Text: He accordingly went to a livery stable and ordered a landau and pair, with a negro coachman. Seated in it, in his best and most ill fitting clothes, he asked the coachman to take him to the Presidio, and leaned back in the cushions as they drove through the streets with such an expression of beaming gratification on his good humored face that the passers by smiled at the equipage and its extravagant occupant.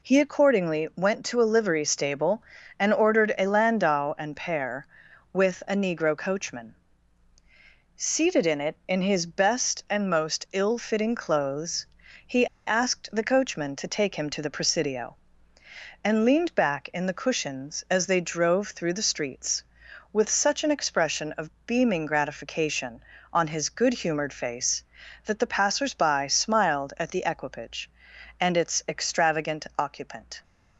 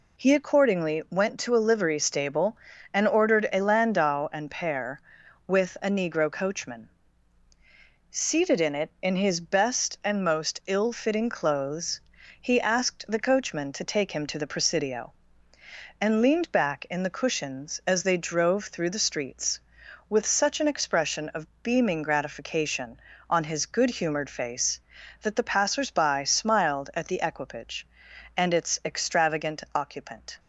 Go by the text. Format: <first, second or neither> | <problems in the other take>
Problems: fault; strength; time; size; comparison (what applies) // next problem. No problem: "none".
second | pauses between "he" and "asked"; slight; at 12.4 s; 0.20 s long